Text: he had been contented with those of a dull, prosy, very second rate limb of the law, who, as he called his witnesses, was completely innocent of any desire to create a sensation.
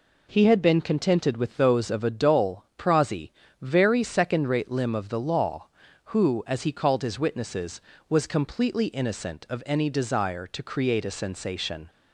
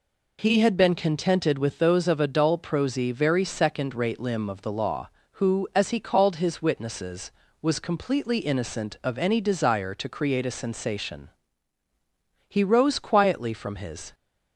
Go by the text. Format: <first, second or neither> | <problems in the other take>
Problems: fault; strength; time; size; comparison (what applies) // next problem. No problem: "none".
first | goes on to say "He rose quietly from his"; from 12.4 s on; 1.6 s long